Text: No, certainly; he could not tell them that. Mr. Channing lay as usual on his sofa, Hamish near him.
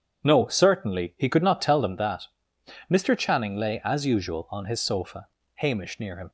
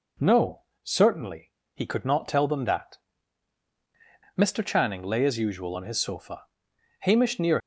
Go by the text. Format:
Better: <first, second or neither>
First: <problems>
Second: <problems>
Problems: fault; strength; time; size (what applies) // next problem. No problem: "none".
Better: first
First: none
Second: stops before "him"; at 7.6 s